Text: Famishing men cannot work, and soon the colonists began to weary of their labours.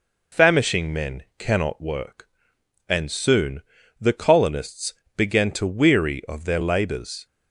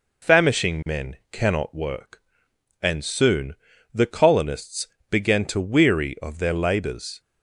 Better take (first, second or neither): neither